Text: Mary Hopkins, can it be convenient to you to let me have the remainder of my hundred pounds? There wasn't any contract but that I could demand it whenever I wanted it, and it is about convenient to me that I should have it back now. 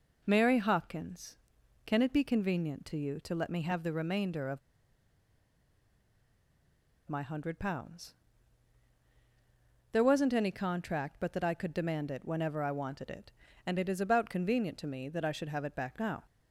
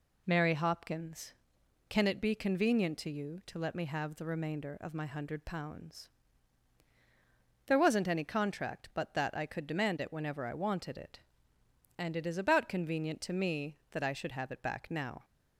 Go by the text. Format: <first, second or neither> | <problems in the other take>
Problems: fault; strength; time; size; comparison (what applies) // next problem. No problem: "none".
second | pauses between "of" and "my"; strong; at 4.5 s; 2.5 s long